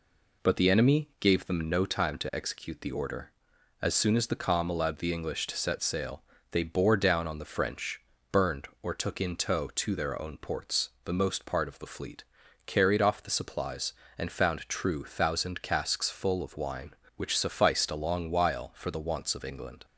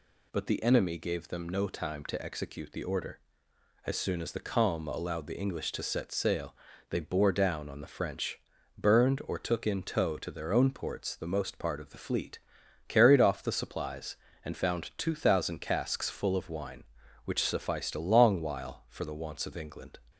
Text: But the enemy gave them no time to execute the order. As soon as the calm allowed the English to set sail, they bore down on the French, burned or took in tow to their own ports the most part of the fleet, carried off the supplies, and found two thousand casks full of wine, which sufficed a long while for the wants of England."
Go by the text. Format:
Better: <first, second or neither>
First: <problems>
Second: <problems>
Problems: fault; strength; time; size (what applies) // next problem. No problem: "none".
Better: second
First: pauses between "ports" and "the"; slight; at 10.8 s; 0.16 s long // says "true" for "two"; at 14.6 s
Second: none